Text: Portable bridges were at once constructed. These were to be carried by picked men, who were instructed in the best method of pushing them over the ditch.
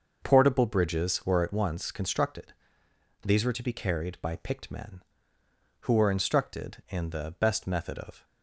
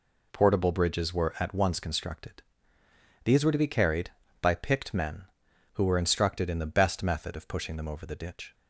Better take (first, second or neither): second